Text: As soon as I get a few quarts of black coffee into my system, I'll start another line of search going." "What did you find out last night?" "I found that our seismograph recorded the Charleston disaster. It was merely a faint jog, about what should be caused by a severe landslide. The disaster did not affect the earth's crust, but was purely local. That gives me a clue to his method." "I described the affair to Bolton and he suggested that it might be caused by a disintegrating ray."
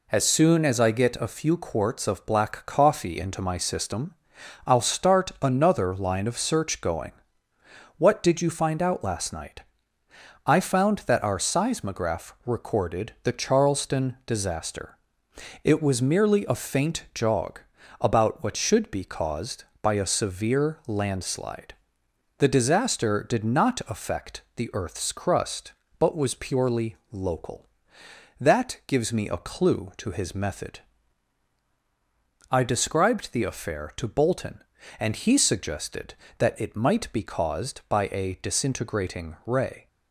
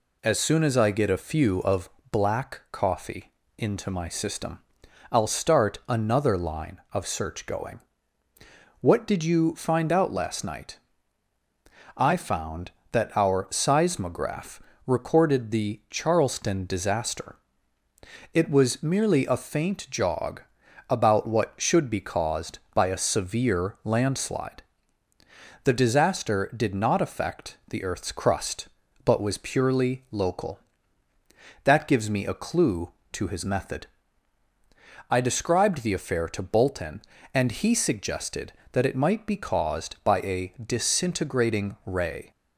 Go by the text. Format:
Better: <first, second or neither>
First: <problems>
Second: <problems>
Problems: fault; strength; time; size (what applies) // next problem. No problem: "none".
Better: first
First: none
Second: skips "quarts"; at 1.6 s // pauses between "of" and "black"; slight; at 1.8 s; 0.22 s long // pauses between "coffee" and "into"; slight; at 3.3 s; 0.26 s long // pauses between "seismograph" and "recorded"; slight; at 14.6 s; 0.24 s long